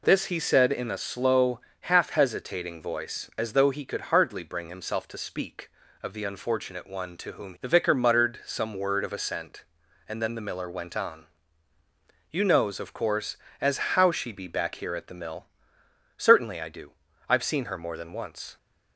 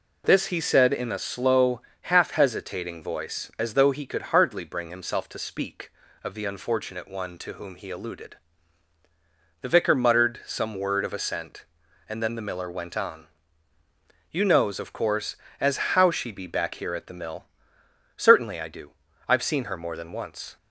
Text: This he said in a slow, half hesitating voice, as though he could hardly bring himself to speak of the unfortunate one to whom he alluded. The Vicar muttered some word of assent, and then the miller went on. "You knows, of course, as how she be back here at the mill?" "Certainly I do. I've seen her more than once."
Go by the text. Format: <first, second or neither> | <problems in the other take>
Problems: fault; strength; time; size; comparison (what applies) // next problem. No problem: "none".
second | skips "he alluded"; at 7.5 s